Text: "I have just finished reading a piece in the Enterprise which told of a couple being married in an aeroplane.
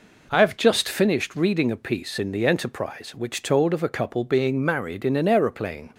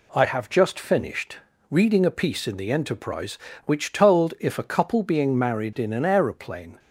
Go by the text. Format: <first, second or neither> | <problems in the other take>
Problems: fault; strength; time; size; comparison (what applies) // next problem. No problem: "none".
first | pauses between "finished" and "reading"; slight; at 1.3 s; 0.34 s long // says "if" for "of"; at 4.4 s